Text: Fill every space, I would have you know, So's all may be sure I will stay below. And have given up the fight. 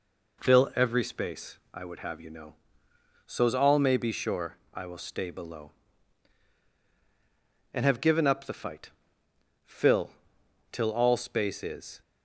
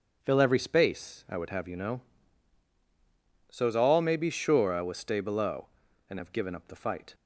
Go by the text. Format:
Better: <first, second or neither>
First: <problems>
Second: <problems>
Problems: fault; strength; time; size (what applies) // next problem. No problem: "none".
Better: second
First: pauses between "sure" and "I"; slight; at 4.5 s; 0.16 s long // goes on to say "Fill till all space is"; strong; from 9.6 s on; 2.3 s long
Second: none